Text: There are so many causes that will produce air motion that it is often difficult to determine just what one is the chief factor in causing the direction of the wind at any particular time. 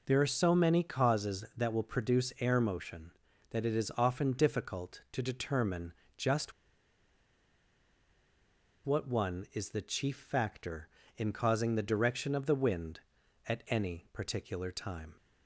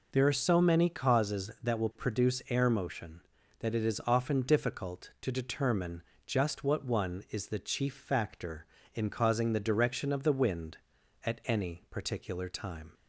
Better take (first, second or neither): second